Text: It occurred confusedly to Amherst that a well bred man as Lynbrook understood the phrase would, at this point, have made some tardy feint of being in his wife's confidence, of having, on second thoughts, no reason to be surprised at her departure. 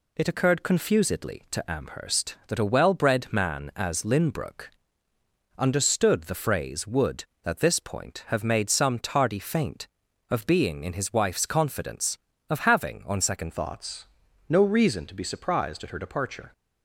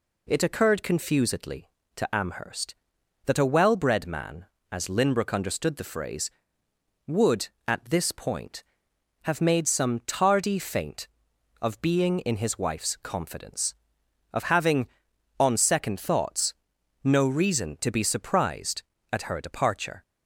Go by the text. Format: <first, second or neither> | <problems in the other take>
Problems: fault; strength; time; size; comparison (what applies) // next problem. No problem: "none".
second | pauses between "Lynbrook" and "understood"; noticeable; at 4.6 s; 0.88 s long // changes voice at "thoughts"; from 13.5 s on; 3.0 s long